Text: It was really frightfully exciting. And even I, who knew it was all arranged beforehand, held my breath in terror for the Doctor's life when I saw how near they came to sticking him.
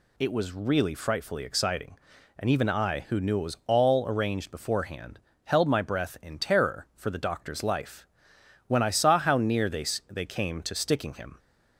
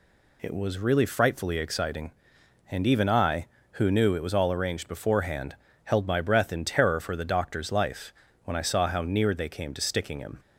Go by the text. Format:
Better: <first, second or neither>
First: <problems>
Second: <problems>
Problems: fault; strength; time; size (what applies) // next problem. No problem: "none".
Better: second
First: pauses between "life" and "when"; noticeable; at 8.0 s; 0.62 s long // says "they" twice; at 10.1 s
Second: pauses between "life" and "when"; slight; at 8.1 s; 0.32 s long